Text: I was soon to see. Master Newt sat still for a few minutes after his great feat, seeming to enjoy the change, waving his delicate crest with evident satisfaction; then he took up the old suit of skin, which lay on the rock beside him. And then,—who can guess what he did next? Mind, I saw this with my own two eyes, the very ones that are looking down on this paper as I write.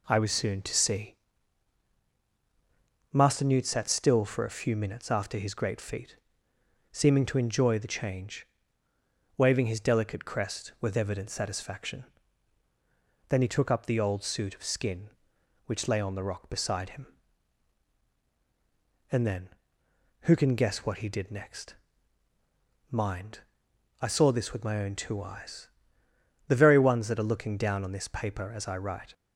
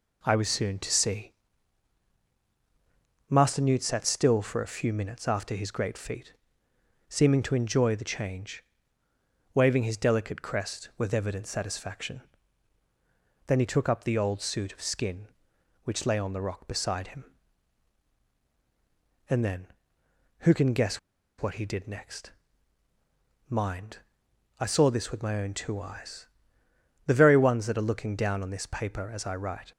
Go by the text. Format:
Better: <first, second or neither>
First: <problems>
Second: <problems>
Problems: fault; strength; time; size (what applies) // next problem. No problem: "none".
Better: first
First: none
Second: pauses between "guess" and "what"; at 20.9 s; 0.41 s long